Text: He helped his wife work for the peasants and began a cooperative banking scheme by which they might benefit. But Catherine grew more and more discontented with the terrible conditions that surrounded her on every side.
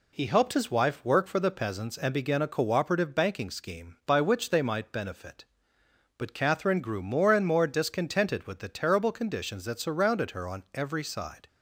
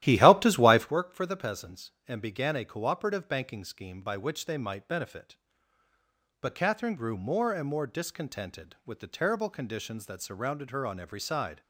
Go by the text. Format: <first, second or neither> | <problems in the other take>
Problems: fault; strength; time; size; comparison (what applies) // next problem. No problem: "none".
first | starts louder than the rest; strong; until 0.9 s; 13.5 dB